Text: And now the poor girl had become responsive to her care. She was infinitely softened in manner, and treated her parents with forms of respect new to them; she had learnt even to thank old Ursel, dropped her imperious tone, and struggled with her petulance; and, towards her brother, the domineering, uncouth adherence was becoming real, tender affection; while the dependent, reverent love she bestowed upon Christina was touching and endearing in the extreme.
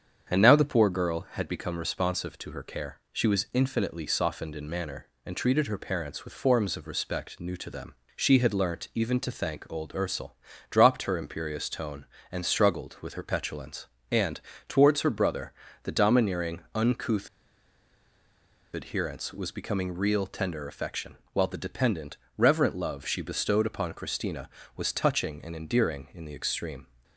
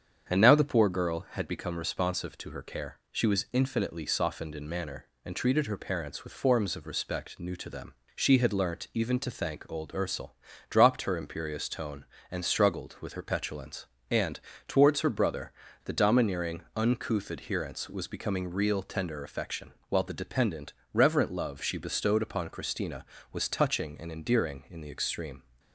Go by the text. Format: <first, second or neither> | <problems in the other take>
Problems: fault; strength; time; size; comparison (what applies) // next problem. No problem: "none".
second | starts louder than the rest; strong; until 1.3 s; 8 dB; strong in the second // pauses between "uncouth" and "adherence"; strong; at 17.2 s; 1.4 s long